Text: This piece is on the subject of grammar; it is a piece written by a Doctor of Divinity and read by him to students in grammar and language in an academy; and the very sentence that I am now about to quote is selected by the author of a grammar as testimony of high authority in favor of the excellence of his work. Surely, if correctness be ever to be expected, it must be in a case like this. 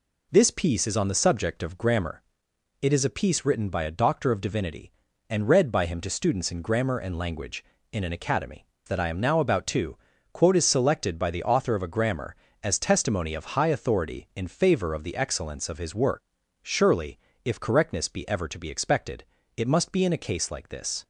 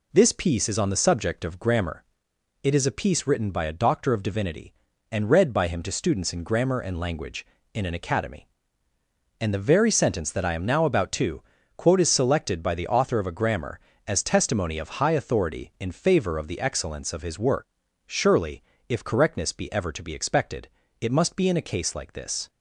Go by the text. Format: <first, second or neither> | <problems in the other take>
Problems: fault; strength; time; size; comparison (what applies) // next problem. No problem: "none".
second | skips "and the very sentence"; at 8.7 s // pauses between "to" and "quote"; slight; at 9.9 s; 0.36 s long; slight in the second